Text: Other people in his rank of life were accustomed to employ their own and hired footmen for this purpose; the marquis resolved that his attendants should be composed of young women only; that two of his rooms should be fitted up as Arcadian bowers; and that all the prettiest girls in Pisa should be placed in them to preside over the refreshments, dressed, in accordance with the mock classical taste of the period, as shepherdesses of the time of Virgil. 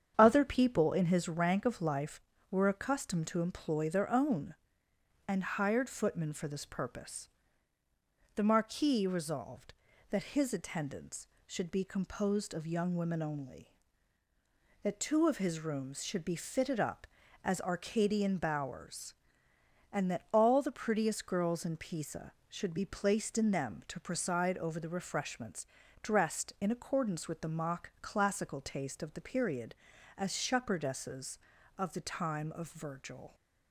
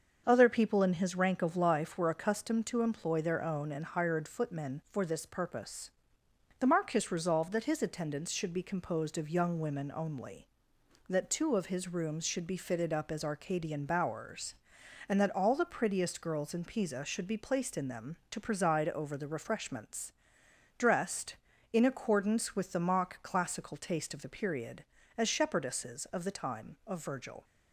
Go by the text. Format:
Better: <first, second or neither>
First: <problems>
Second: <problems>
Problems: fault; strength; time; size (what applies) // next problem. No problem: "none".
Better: neither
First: starts louder than the rest; strong; until 1.1 s; 8 dB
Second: starts louder than the rest; until 1.2 s; 6.5 dB